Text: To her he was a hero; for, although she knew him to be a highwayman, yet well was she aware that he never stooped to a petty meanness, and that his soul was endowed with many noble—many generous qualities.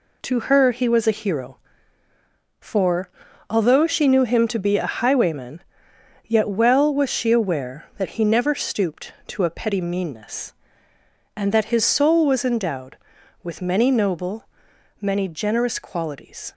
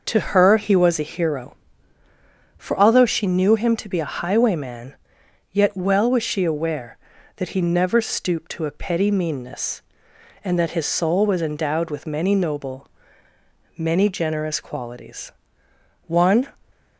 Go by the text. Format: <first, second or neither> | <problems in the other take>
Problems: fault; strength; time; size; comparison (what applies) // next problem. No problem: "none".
first | goes on to say "One"; slight; from 16.0 s on; 0.42 s long